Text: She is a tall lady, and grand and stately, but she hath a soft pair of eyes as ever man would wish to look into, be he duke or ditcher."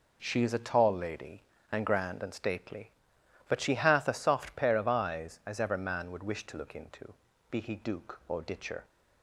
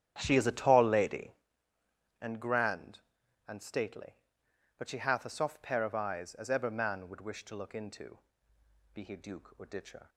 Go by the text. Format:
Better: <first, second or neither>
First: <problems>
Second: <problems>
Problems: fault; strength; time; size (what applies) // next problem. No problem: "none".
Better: first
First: none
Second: starts louder than the rest; strong; until 1.4 s; 10.5 dB